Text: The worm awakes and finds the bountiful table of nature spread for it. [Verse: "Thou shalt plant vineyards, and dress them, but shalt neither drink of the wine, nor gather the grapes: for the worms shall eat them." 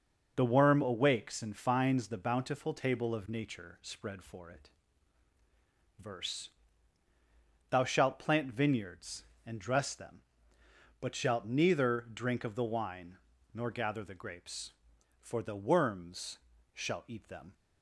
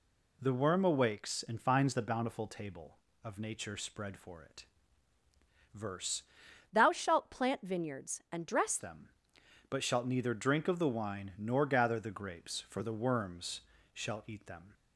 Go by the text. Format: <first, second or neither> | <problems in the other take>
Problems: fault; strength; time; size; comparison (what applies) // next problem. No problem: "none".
first | changes voice from "Thou" to "dress"; from 6.7 to 8.7 s; 2.0 s long // pauses between "worms" and "shall"; slight; at 13.6 s; 0.32 s long; slight in the first